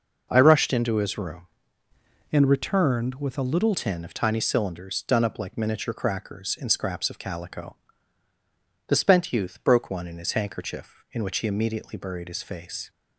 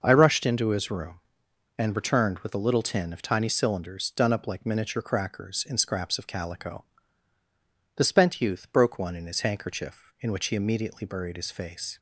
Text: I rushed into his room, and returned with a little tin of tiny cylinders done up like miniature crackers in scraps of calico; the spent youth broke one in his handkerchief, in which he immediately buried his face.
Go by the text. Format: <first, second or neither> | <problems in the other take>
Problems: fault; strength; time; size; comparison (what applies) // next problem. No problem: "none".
second | changes voice from "and" to "little"; from 2.3 to 3.7 s; 1.4 s long